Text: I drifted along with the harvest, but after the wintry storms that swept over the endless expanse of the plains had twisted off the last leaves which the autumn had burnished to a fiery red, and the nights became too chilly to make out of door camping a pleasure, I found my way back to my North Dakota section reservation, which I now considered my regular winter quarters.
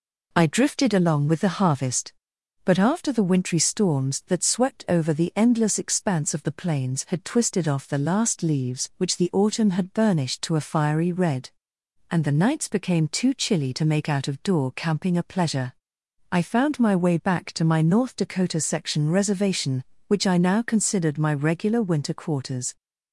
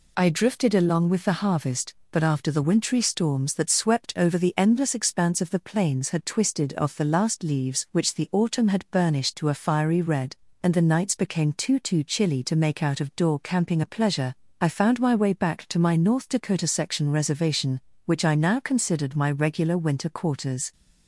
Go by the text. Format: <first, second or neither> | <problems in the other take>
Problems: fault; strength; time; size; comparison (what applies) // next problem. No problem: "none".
first | says "too" twice; at 11.7 s